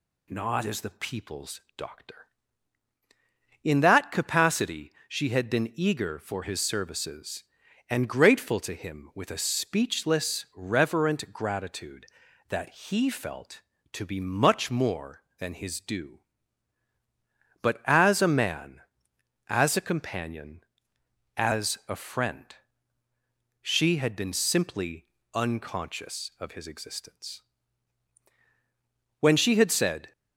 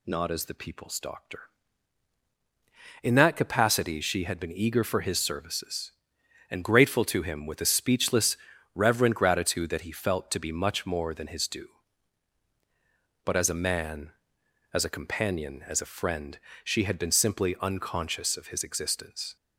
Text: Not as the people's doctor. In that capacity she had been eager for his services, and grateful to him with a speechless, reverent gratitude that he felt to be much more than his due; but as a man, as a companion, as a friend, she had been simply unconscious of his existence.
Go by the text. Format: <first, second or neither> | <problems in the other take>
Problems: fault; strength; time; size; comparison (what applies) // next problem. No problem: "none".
second | pauses between "people's" and "doctor"; slight; at 1.5 s; 0.16 s long // pauses between "capacity" and "she"; slight; at 4.9 s; 0.16 s long // pauses between "simply" and "unconscious"; slight; at 25.0 s; 0.28 s long // goes on to say "When she had said"; noticeable; from 29.1 s on; 0.92 s long